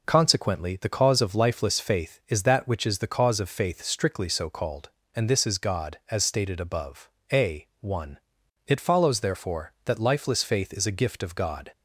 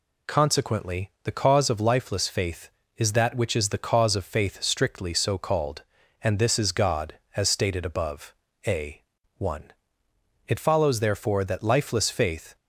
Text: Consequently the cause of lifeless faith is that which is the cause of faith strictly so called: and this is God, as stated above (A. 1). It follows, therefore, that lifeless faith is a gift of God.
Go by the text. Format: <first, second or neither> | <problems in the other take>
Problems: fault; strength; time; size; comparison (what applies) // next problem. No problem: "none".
first | stops before "is a gift of God"; at 12.5 s